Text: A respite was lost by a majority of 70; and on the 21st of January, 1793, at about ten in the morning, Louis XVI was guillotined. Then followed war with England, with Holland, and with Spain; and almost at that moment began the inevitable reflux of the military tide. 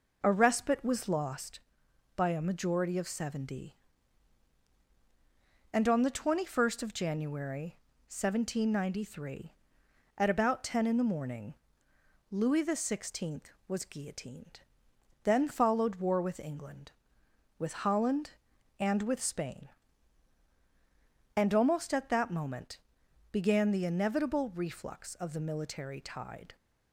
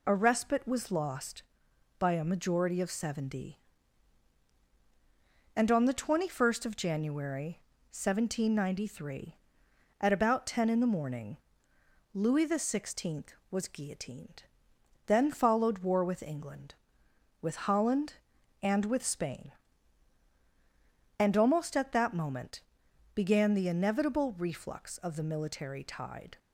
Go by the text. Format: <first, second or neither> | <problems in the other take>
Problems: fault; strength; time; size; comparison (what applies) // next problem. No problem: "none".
second | starts louder than the rest; noticeable; until 1.4 s; 5 dB // pauses between "moment" and "began"; noticeable; at 22.7 s; 0.52 s long; noticeable in the second